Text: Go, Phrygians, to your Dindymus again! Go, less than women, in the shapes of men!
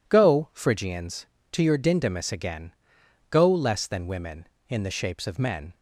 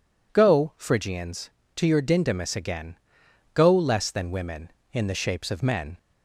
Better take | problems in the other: second | gets quieter; strong; throughout; 8.5 dB

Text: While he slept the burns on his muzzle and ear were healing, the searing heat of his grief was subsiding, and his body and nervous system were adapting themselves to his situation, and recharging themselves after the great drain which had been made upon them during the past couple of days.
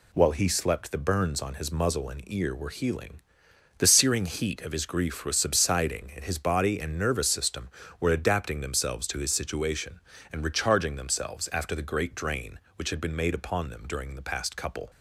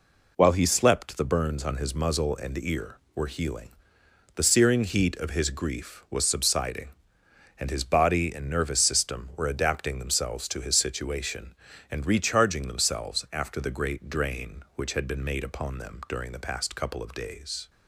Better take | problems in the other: second | stops before "of days"; at 14.8 s

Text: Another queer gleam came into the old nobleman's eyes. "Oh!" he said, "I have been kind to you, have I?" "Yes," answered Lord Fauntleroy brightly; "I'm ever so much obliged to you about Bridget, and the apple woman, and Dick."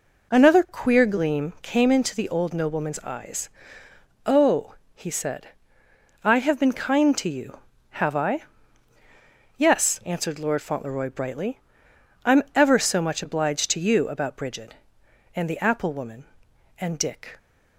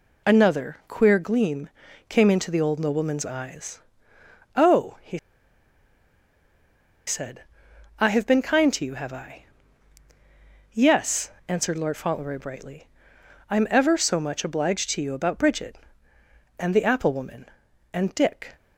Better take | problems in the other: first | pauses between "gleam" and "came"; at 1.6 s; 0.40 s long // pauses between "he" and "said"; strong; at 5.1 s; 1.8 s long

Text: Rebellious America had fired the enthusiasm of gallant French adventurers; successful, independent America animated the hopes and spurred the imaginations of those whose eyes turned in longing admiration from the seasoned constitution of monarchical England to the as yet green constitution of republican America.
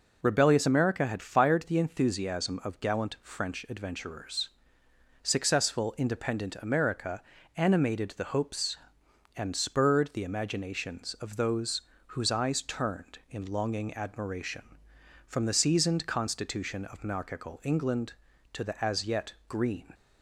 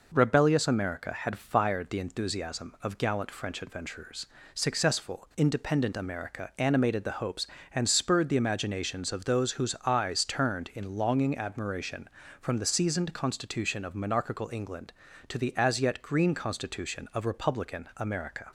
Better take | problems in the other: second | pauses between "America" and "animated"; slight; at 7.2 s; 0.34 s long // pauses between "those" and "whose"; slight; at 11.8 s; 0.26 s long // pauses between "yet" and "green"; slight; at 19.3 s; 0.16 s long // stops before "constitution of republican America"; at 19.9 s

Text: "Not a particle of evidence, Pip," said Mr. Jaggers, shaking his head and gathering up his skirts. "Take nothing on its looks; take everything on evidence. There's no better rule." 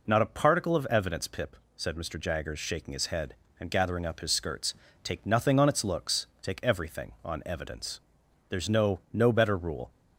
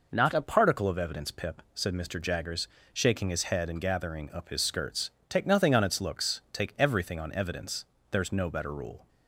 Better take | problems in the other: second | says "no" twice; at 9.1 s

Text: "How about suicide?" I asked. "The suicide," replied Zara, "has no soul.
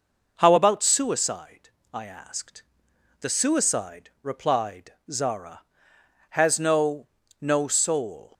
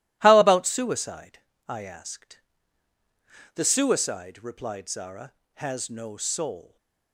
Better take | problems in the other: second | pauses between "replied" and "Zara"; slight; at 4.9 s; 0.18 s long // says "no" twice; at 7.3 s

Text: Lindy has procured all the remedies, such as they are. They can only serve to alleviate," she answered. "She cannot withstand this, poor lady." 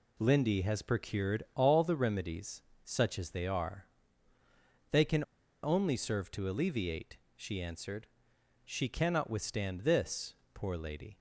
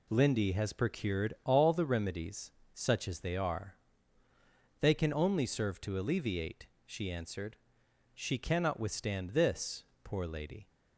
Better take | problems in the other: second | pauses between "can" and "only"; at 5.2 s; 0.38 s long

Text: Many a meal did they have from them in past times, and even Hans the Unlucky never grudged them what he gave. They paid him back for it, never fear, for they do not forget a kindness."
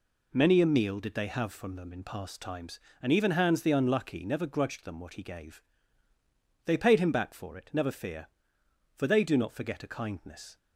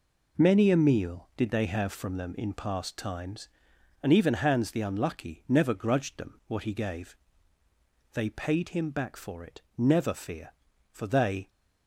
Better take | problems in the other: first | stops before "do not forget a kindness"; at 11.4 s

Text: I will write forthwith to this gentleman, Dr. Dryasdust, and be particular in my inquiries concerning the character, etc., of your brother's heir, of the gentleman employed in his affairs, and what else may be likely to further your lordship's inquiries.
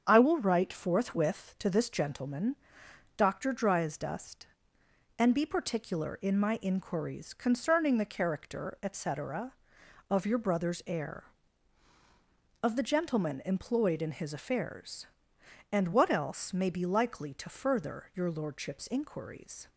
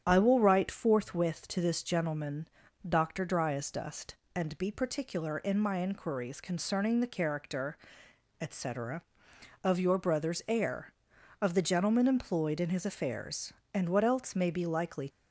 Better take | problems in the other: first | starts louder than the rest; strong; until 1.0 s; 9 dB; strong in the first // stops before "to further your lordship's inquiries"; at 15.0 s

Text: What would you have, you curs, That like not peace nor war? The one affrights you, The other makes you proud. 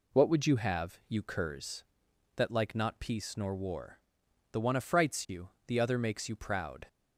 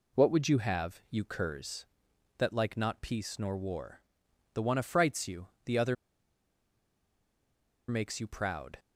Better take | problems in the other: first | pauses between "other" and "makes"; strong; at 5.9 s; 1.9 s long

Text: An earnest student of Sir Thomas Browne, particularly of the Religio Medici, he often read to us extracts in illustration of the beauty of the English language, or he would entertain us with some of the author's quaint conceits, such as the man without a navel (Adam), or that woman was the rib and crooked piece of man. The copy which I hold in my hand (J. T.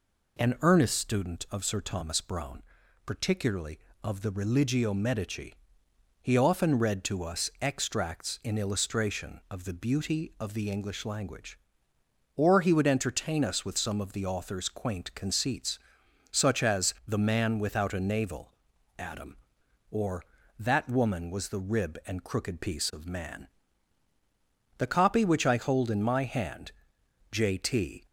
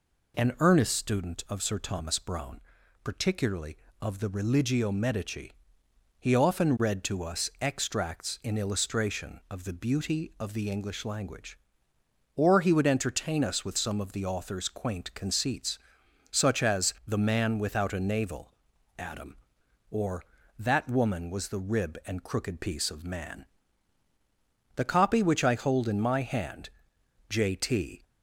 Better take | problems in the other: neither | none

